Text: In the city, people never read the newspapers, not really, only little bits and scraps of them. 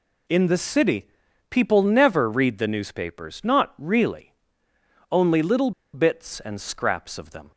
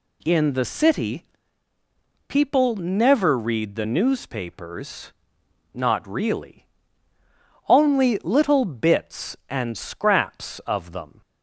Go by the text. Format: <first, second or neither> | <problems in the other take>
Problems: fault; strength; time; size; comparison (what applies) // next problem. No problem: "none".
second | pauses between "little" and "bits"; slight; at 5.7 s; 0.22 s long